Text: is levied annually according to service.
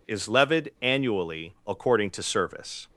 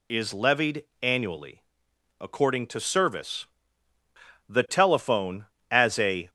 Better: first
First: none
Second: pauses between "levied" and "annually"; slight; at 0.8 s; 0.18 s long // pauses between "annually" and "according"; noticeable; at 1.6 s; 0.58 s long // goes on to say "The telephone as a"; strong; from 4.4 s on; 1.8 s long

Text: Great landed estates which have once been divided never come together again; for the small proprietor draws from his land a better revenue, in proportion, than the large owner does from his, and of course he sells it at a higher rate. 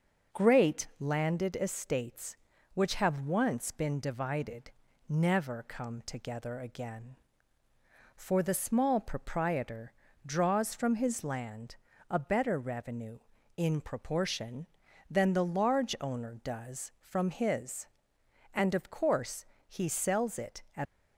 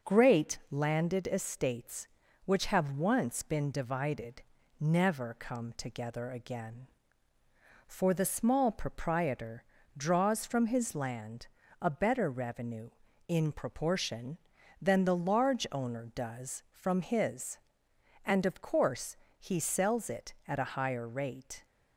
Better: second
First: starts louder than the rest; noticeable; until 1.4 s; 6 dB // pauses between "divided" and "never"; at 4.7 s; 0.38 s long // pauses between "proprietor" and "draws"; slight; at 9.9 s; 0.32 s long // pauses between "land" and "a"; slight; at 11.7 s; 0.34 s long // pauses between "course" and "he"; slight; at 19.4 s; 0.20 s long // stops before "a higher rate"; at 20.8 s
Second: pauses between "divided" and "never"; at 4.4 s; 0.38 s long // pauses between "proprietor" and "draws"; slight; at 9.6 s; 0.32 s long // pauses between "land" and "a"; slight; at 11.4 s; 0.34 s long // pauses between "course" and "he"; slight; at 19.1 s; 0.20 s long

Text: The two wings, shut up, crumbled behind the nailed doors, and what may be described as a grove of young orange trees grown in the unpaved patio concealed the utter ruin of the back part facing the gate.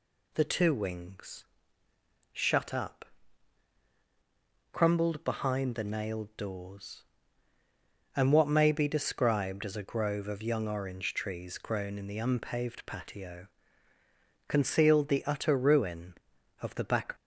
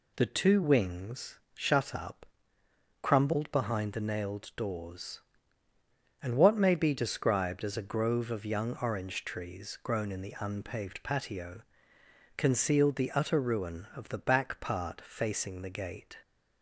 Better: second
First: pauses between "patio" and "concealed"; noticeable; at 13.4 s; 0.98 s long // stops before "part facing the gate"; at 17.1 s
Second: pauses between "patio" and "concealed"; noticeable; at 11.6 s; 0.74 s long

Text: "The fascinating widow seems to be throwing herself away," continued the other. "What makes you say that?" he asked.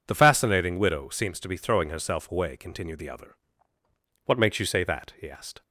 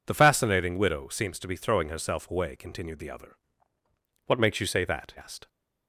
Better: first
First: none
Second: skips "he"; at 5.1 s

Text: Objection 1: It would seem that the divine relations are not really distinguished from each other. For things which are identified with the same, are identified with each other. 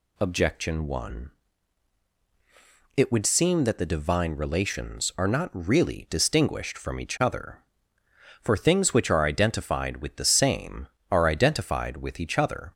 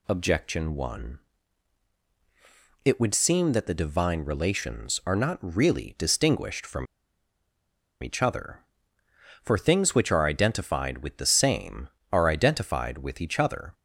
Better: first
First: none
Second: pauses between "from" and "each"; at 6.8 s; 1.1 s long

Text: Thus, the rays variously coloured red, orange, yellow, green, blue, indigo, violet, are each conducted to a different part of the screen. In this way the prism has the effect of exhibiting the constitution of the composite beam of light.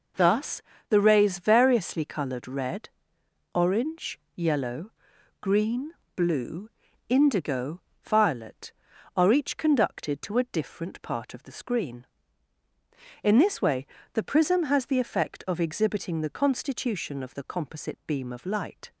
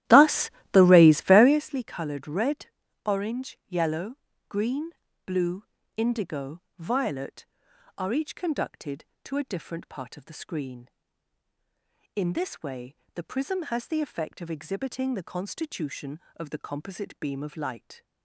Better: first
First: pauses between "way" and "the"; slight; at 13.8 s; 0.28 s long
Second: starts louder than the rest; strong; until 1.6 s; 13.5 dB // pauses between "way" and "the"; slight; at 12.9 s; 0.20 s long

